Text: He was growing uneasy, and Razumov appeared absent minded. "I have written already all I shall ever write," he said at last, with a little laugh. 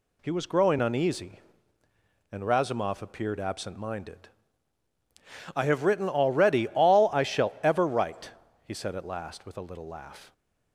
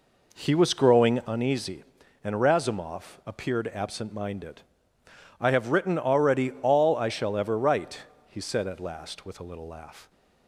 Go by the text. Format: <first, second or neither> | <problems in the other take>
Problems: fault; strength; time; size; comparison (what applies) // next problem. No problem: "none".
first | starts louder than the rest; noticeable; until 1.3 s; 4 dB